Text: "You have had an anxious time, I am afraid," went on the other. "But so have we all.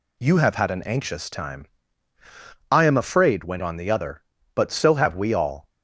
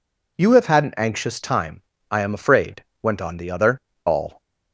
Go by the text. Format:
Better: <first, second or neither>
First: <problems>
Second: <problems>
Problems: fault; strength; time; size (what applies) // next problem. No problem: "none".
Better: first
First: none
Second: skips "But so have we"; at 3.9 s